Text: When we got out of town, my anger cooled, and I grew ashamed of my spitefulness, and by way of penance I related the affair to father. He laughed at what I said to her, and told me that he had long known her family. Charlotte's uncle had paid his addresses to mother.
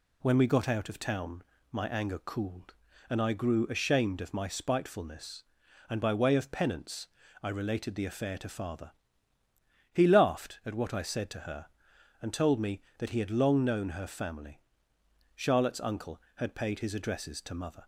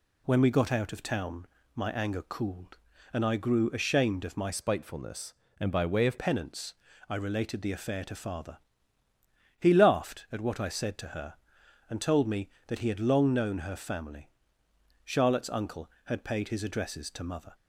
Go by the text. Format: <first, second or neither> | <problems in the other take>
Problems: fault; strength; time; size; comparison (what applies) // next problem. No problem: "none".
first | changes voice from "spitefulness" to "of"; from 4.5 to 6.1 s; 1.6 s long // pauses between "penance" and "I"; slight; at 6.7 s; 0.36 s long; slight in the first